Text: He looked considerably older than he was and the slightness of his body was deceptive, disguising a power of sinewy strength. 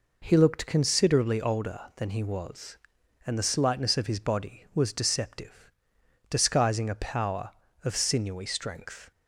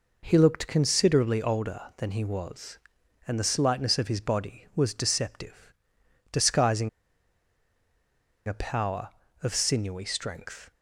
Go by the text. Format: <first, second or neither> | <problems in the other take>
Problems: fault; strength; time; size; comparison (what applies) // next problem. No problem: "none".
first | pauses between "disguising" and "a"; strong; at 6.8 s; 1.5 s long